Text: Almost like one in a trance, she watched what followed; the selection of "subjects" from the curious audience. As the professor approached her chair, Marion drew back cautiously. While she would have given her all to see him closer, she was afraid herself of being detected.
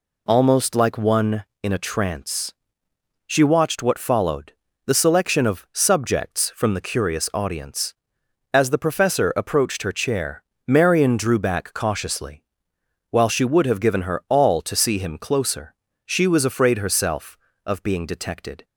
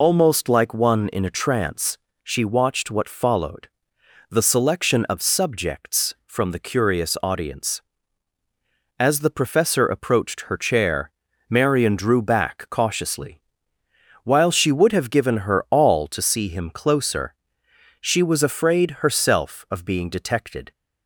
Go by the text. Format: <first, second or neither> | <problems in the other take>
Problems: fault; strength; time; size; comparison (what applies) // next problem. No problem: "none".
first | loses the start of "Almost"; at 0.0 s; 70 ms